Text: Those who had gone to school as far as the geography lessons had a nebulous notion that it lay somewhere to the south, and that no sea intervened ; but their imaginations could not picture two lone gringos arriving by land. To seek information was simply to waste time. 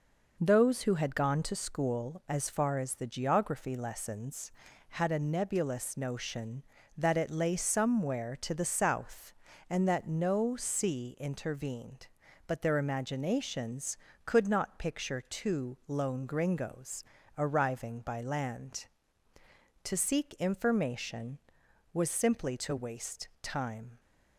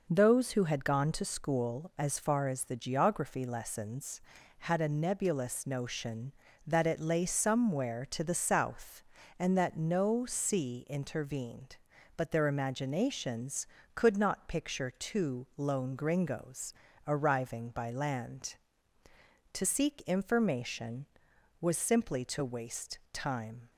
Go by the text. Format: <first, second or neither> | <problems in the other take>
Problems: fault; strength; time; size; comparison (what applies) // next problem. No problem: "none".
neither | pauses between "gringos" and "arriving"; slight; the same in both